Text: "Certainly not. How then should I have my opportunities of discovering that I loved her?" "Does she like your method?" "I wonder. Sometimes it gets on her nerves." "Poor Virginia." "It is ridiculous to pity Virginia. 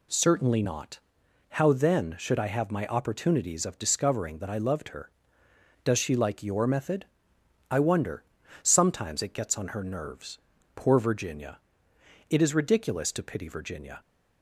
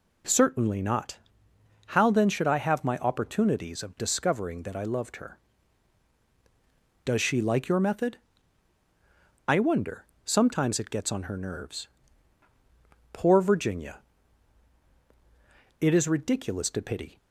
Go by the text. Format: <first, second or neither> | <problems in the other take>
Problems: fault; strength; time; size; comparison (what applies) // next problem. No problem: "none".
first | stops before "Virginia"; at 17.1 s